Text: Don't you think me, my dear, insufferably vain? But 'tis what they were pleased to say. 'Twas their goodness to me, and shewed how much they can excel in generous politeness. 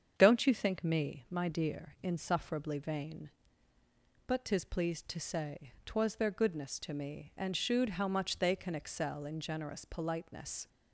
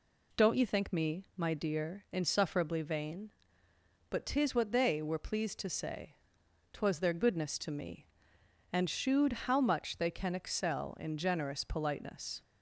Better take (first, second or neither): second